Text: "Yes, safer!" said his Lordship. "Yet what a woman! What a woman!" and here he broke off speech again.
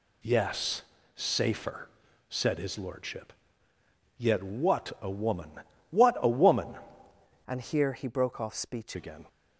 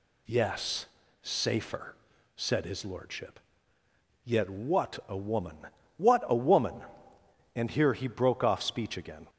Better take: second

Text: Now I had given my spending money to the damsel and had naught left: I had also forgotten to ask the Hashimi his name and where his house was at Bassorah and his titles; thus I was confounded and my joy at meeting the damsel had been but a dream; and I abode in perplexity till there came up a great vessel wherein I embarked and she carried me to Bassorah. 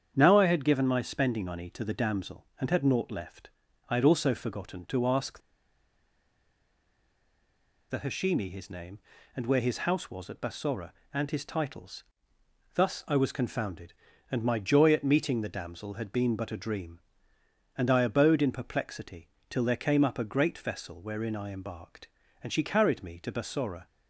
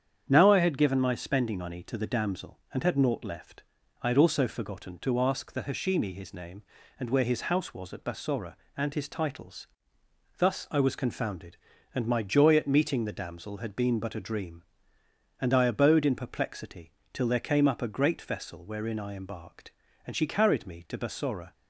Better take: second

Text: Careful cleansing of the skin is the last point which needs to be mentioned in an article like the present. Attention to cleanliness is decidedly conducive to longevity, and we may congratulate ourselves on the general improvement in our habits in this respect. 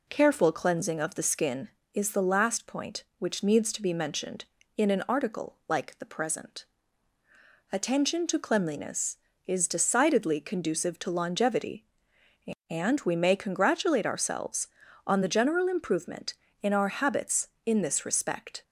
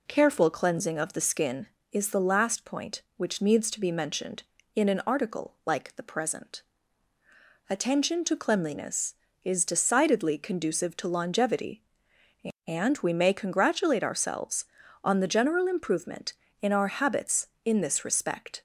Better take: neither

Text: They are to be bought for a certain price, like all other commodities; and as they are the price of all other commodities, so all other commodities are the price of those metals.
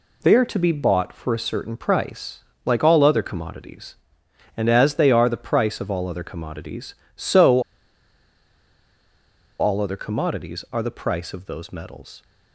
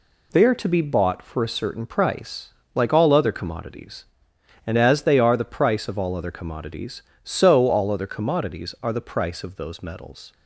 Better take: second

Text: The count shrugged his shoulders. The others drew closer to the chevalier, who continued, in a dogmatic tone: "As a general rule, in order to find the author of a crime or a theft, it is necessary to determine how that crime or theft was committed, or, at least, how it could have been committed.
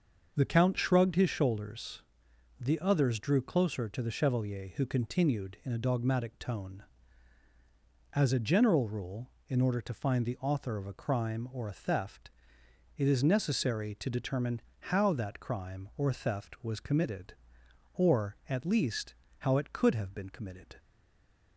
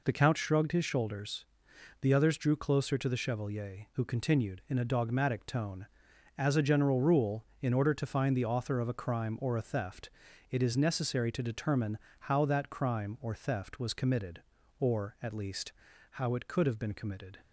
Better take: second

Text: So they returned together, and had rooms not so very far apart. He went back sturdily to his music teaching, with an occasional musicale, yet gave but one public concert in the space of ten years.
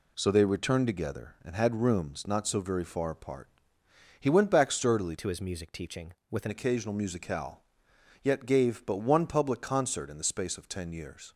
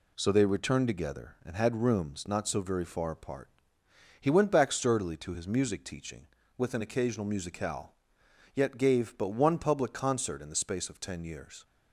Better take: second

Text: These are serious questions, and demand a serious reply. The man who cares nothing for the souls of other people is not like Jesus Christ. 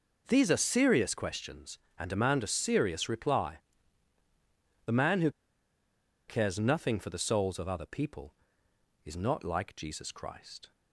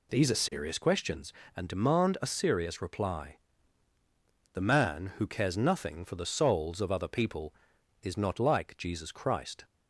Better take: second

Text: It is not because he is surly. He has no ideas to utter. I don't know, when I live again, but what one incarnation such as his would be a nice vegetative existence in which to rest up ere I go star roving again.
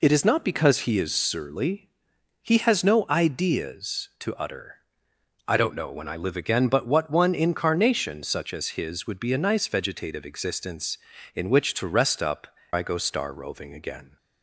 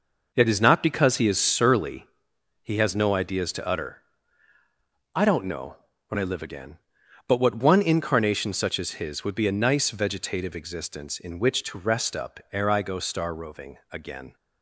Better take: second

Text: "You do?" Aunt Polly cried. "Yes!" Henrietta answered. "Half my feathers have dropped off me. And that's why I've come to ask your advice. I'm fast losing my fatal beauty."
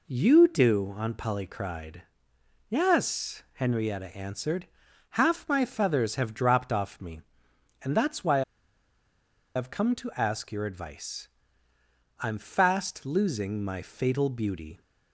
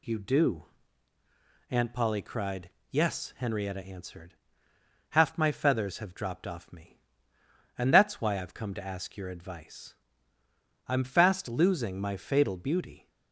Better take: second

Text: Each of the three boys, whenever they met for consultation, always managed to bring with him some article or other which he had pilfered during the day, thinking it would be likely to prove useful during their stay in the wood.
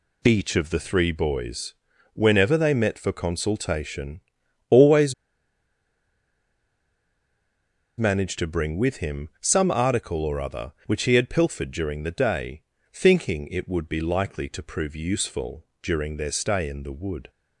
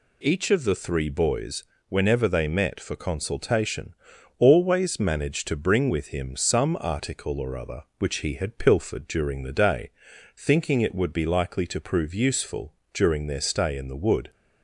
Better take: second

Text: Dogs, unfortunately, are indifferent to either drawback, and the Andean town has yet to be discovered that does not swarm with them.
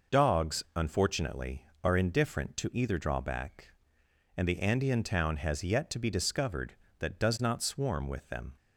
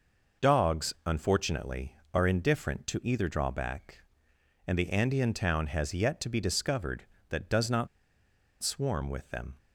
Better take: first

